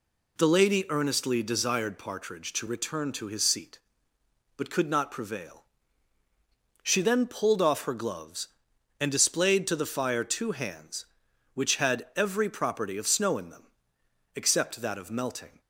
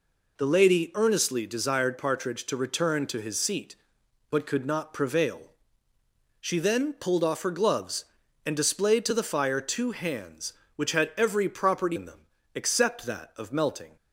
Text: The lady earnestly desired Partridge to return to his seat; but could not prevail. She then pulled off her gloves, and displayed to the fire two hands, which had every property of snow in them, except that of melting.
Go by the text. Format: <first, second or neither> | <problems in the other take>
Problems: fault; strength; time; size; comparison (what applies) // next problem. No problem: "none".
first | skips "of snow"; at 11.9 s